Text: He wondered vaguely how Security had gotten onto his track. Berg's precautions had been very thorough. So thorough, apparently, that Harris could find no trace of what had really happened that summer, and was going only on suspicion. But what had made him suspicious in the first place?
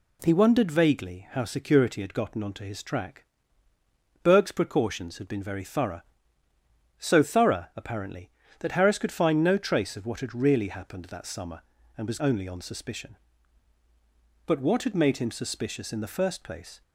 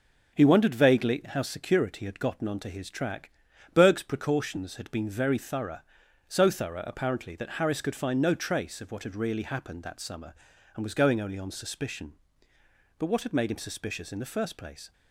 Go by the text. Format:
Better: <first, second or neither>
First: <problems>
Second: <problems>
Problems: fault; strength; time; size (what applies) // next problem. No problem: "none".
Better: second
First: skips "going"; at 12.1 s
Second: none